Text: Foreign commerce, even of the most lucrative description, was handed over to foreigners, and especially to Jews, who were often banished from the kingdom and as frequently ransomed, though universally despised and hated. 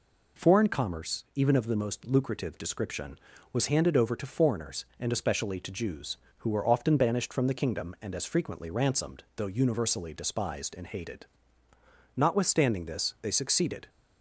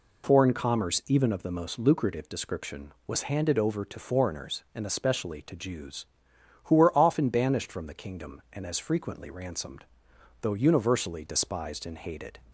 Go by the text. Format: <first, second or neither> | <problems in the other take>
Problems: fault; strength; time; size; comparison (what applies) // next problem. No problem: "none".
second | goes on to say "Notwithstanding this they succeeded"; strong; from 12.1 s on; 1.7 s long